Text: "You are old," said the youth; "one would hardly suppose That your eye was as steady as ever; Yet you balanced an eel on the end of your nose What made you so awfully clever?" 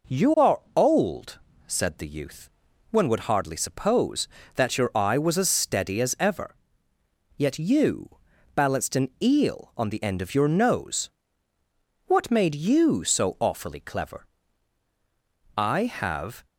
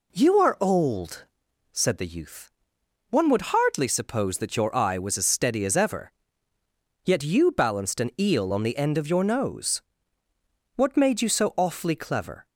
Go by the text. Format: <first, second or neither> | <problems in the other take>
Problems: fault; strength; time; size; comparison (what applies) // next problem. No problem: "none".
second | pauses between "you" and "balanced"; at 8.1 s; 0.40 s long // pauses between "nose" and "What"; noticeable; at 11.0 s; 0.96 s long; noticeable in the second // goes on to say "I have"; noticeable; from 15.5 s on; 0.88 s long